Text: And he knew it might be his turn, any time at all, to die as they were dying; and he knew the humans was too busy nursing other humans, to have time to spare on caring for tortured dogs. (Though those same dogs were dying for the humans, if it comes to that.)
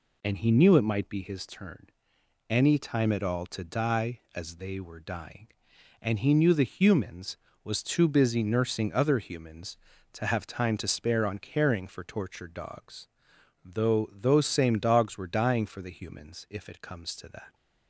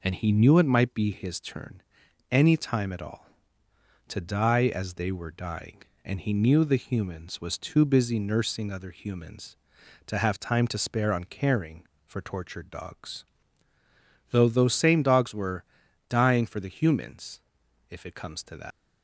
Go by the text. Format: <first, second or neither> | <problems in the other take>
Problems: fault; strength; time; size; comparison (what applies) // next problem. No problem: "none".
first | pauses between "were" and "dying"; at 15.6 s; 0.44 s long // leaves "that" unfinished; at 18.7 s; 100 ms